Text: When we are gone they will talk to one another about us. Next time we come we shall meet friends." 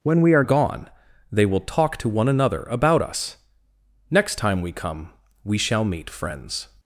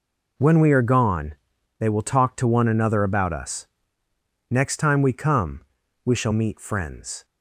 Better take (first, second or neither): second